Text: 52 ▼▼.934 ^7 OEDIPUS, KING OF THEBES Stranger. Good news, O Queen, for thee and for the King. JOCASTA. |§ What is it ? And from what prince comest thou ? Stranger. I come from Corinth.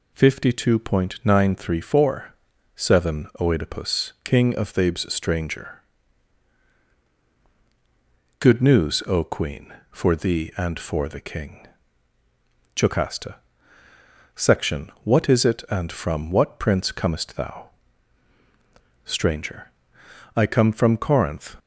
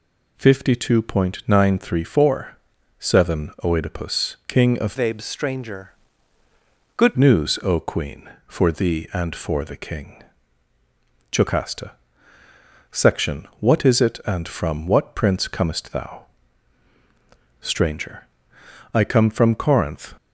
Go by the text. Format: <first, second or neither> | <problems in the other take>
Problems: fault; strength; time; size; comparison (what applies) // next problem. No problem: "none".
first | changes voice from "THEBES" to "Good"; from 4.9 to 7.1 s; 2.2 s long